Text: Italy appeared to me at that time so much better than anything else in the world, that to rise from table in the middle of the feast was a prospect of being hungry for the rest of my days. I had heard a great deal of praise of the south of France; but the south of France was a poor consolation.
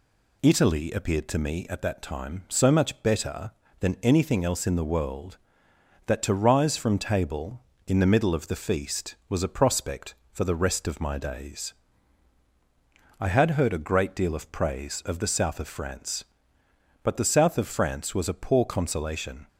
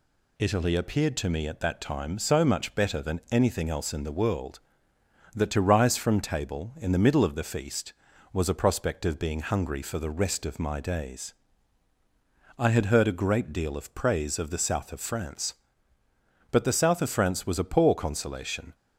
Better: second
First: skips "of being hungry"; at 10.2 s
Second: none

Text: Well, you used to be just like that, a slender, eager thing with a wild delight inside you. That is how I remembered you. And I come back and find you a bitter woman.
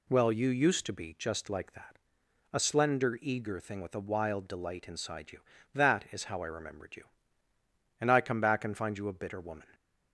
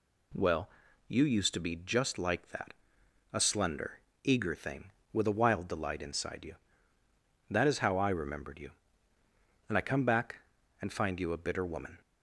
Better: neither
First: none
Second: none

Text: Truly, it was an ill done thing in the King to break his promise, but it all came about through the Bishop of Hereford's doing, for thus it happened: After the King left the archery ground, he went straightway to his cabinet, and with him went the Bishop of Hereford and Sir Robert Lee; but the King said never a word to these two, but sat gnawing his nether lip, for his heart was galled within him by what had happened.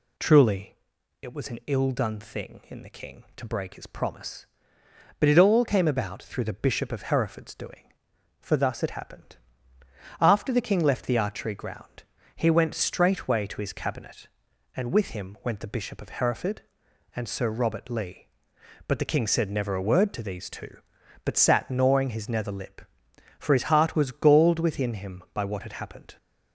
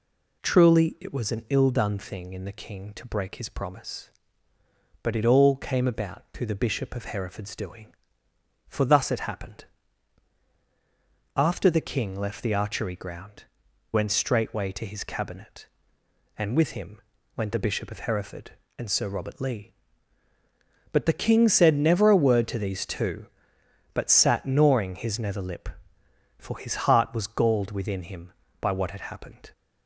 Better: first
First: none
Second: skips "he"; at 13.6 s // pauses between "him" and "went"; slight; at 16.9 s; 0.36 s long // pauses between "his" and "heart"; slight; at 26.7 s; 0.16 s long

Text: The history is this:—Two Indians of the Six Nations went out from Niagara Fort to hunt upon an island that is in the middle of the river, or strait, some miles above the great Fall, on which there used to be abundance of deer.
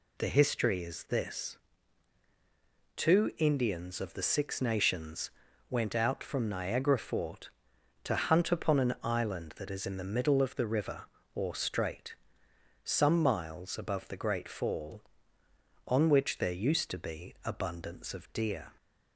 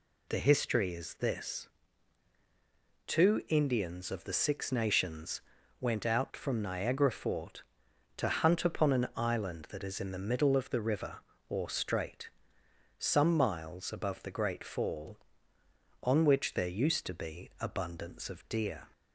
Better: neither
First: pauses between "Nations" and "went"; at 5.2 s; 0.40 s long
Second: pauses between "Nations" and "went"; at 5.3 s; 0.40 s long

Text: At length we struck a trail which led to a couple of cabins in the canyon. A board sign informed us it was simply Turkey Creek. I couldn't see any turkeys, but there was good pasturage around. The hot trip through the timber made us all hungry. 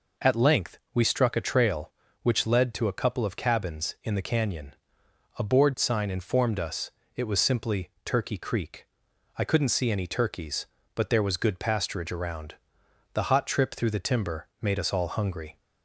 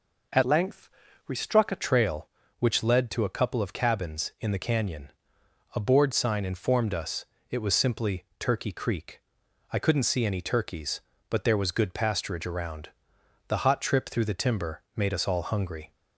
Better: first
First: pauses between "us" and "it"; slight; at 6.9 s; 0.24 s long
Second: changes voice from "length" to "a"; from 0.4 to 1.8 s; 1.4 s long // pauses between "length" and "we"; at 0.8 s; 0.40 s long // pauses between "us" and "it"; slight; at 7.2 s; 0.24 s long

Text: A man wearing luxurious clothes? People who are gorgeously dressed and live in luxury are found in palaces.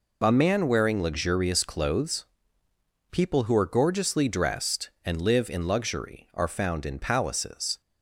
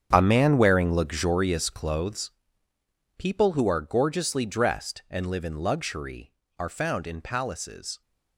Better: first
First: none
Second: gets quieter; strong; throughout; 14 dB

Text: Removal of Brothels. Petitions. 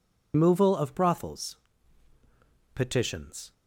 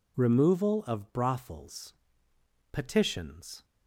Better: second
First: loses the start of "Removal"; at 0.3 s; 145 ms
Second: none

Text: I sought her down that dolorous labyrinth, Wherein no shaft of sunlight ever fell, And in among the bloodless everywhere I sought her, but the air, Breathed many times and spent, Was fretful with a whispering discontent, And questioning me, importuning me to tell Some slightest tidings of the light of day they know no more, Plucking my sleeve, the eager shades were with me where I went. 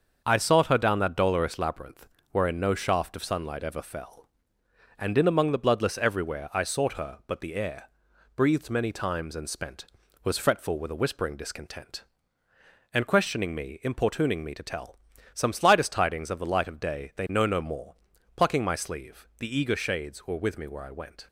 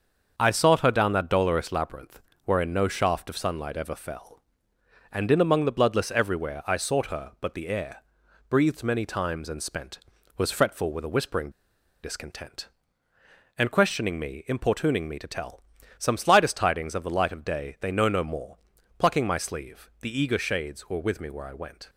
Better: first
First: starts louder than the rest; until 1.2 s; 6.5 dB // pauses between "tell" and "Some"; slight; at 14.9 s; 0.36 s long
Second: starts louder than the rest; until 1.3 s; 6.5 dB // pauses between "whispering" and "discontent"; noticeable; at 11.5 s; 0.52 s long // pauses between "tell" and "Some"; slight; at 15.6 s; 0.36 s long

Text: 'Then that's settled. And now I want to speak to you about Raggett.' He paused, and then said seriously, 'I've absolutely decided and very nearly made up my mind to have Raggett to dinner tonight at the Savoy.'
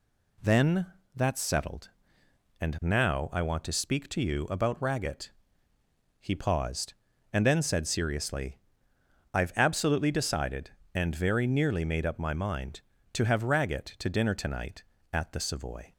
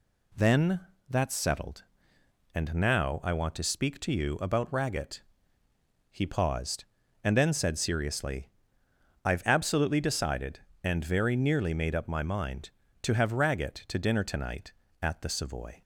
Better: neither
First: pauses between "Then" and "that's"; slight; at 0.8 s; 0.30 s long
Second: pauses between "Then" and "that's"; slight; at 0.7 s; 0.30 s long

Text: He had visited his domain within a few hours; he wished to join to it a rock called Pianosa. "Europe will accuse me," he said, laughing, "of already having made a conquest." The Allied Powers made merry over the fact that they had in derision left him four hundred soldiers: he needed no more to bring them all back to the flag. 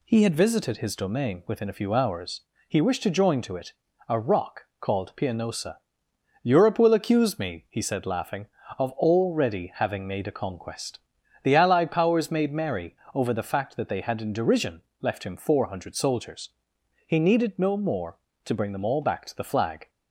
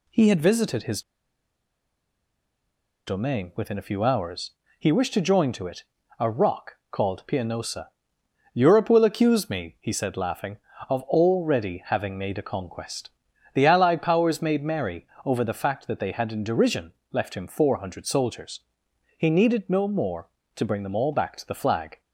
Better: first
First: pauses between "it" and "a"; slight; at 3.7 s; 0.34 s long // pauses between "rock" and "called"; slight; at 4.6 s; 0.16 s long // pauses between "merry" and "over"; slight; at 12.9 s; 0.18 s long // pauses between "derision" and "left"; slight; at 14.8 s; 0.18 s long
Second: pauses between "his" and "domain"; strong; at 1.0 s; 2.0 s long // pauses between "it" and "a"; slight; at 5.8 s; 0.34 s long // pauses between "rock" and "called"; slight; at 6.7 s; 0.16 s long // pauses between "merry" and "over"; slight; at 15.0 s; 0.18 s long // pauses between "derision" and "left"; slight; at 16.9 s; 0.18 s long

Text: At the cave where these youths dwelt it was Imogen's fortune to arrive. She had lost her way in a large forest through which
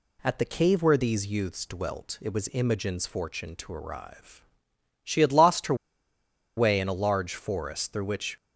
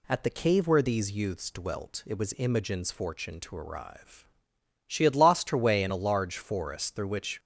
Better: second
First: pauses between "her" and "way"; noticeable; at 5.7 s; 0.82 s long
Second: none

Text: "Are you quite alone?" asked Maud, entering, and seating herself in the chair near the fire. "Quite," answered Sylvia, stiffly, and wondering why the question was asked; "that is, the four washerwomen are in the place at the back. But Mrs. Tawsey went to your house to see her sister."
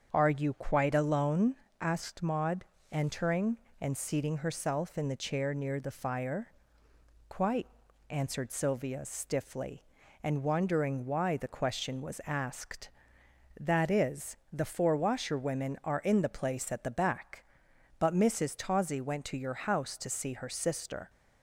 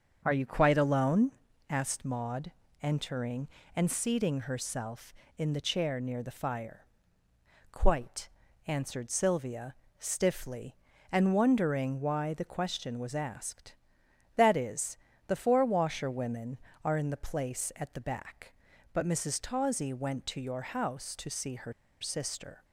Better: first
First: starts louder than the rest; until 1.1 s; 7 dB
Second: starts louder than the rest; until 1.2 s; 7 dB // pauses between "her" and "sister"; slight; at 21.7 s; 0.28 s long

